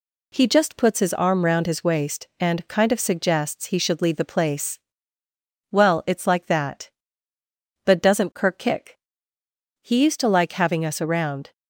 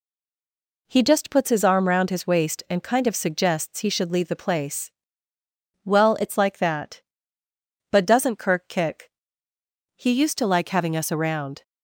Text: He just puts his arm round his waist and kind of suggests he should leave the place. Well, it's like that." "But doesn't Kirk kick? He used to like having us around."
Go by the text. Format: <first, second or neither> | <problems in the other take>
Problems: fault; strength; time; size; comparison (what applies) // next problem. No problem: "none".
first | stays silent before the first word; slight; until 0.8 s; 0.8 s long